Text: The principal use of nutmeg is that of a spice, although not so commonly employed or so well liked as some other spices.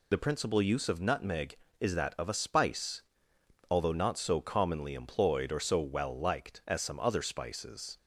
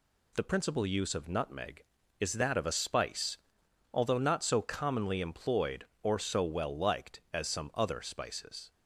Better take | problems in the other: second | loses the start of "The"; at 0.1 s; 45 ms

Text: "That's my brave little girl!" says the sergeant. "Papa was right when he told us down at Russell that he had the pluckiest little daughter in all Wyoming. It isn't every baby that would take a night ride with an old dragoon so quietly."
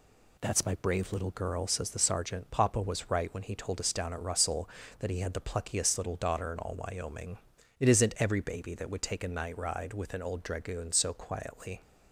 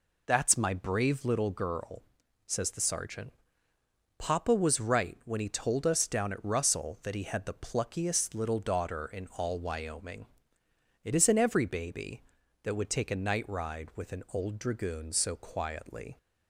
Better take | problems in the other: neither | none

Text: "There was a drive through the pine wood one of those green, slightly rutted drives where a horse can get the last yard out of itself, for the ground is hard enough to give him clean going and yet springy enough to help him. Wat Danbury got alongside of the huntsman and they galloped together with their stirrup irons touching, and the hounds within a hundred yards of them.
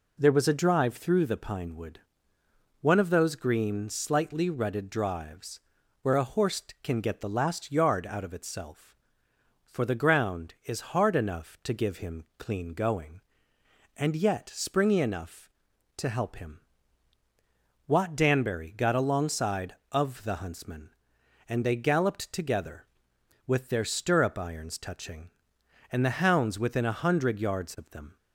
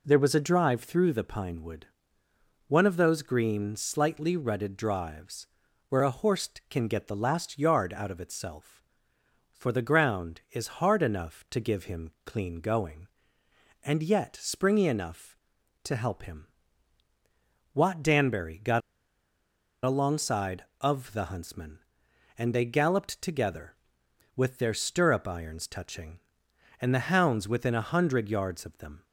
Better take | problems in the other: first | pauses between "wood" and "one"; noticeable; at 1.8 s; 0.80 s long; noticeable in the first // pauses between "drives" and "where"; at 5.4 s; 0.42 s long; also in the first // pauses between "got" and "alongside"; at 18.8 s; 1.0 s long

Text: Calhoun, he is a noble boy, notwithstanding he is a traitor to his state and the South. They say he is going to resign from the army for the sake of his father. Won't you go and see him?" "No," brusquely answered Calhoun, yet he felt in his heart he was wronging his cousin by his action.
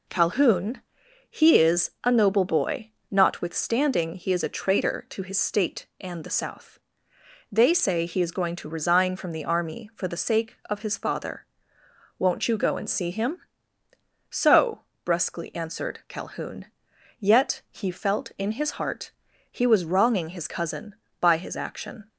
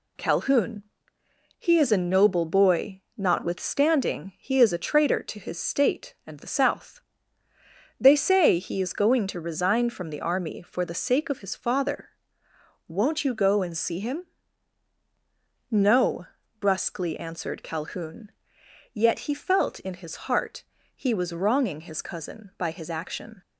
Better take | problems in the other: second | says "So" for "No"; at 14.3 s // pauses between "heart" and "he"; at 19.1 s; 0.40 s long; slight in the second

